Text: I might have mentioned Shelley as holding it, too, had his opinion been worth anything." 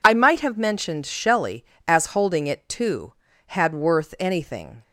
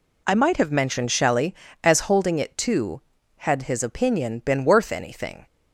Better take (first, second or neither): second